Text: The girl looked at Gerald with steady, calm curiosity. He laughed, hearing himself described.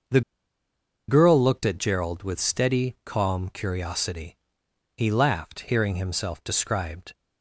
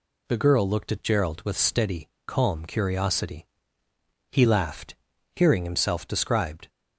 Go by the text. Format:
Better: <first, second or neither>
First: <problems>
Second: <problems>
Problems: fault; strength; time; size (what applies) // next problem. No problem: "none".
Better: second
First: pauses between "The" and "girl"; noticeable; at 0.2 s; 0.87 s long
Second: none